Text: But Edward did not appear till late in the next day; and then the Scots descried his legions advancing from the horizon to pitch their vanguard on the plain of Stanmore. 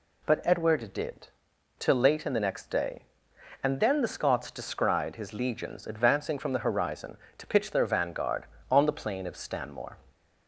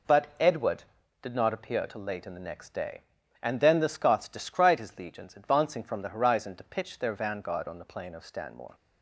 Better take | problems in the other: second | skips "not appear"; at 1.5 s

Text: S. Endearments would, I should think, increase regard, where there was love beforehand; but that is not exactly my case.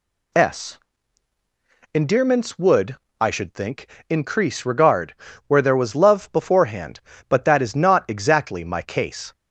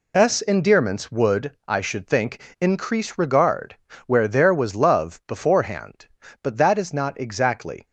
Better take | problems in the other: first | stops before "my case"; at 7.8 s

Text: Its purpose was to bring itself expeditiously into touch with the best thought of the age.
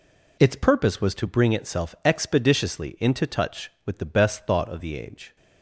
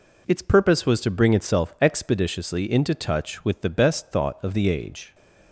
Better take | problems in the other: neither | none

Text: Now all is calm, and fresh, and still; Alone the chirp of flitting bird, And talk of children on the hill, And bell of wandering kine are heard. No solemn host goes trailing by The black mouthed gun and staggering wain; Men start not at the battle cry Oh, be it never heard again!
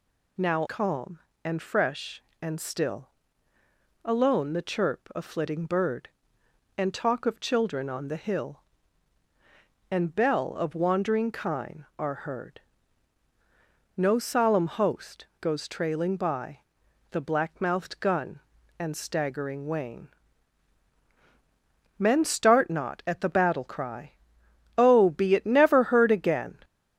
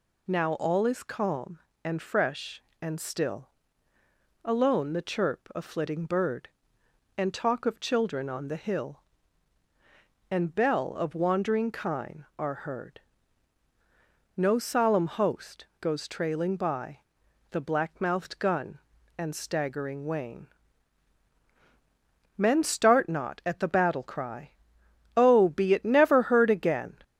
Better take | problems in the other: second | skips "all is"; at 0.6 s // pauses between "by" and "The"; noticeable; at 16.5 s; 0.50 s long; noticeable in the second // pauses between "cry" and "Oh"; noticeable; at 24.1 s; 0.66 s long; noticeable in the second

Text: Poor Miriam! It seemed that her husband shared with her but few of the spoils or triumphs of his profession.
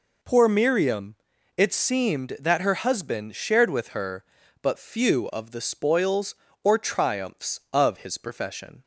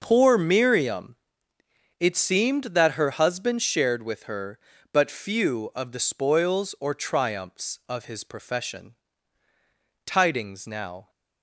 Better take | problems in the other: first | starts louder than the rest; until 1.0 s; 6 dB // goes on to say "Tidings now"; noticeable; from 10.0 s on; 1.0 s long

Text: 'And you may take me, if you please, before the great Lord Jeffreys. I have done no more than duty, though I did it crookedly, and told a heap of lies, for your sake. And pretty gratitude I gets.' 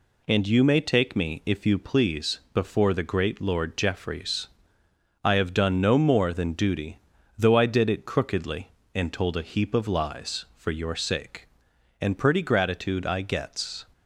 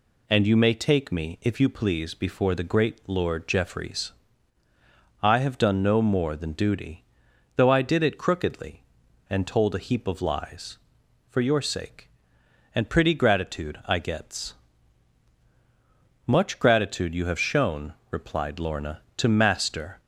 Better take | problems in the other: first | goes on to say "Much gratitude you have shown replied Lorna to Master"; strong; from 16.2 s on; 3.7 s long

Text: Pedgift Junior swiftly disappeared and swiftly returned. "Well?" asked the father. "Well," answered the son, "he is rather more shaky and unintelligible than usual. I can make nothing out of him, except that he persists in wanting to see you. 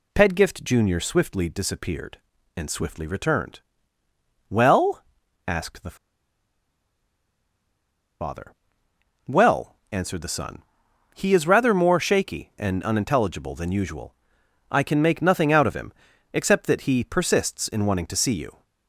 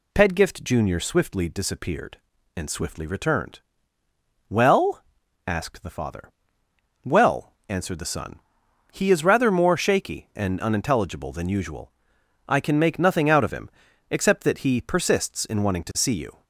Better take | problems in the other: second | pauses between "the" and "father"; strong; at 5.9 s; 2.2 s long

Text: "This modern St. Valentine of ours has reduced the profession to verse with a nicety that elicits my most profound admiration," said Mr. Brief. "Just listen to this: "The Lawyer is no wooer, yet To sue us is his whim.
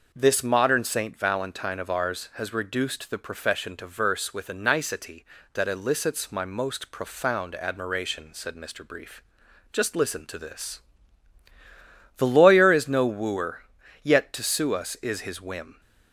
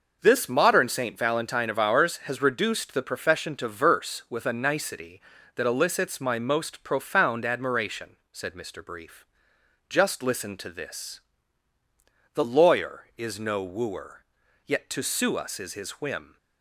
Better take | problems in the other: neither | none

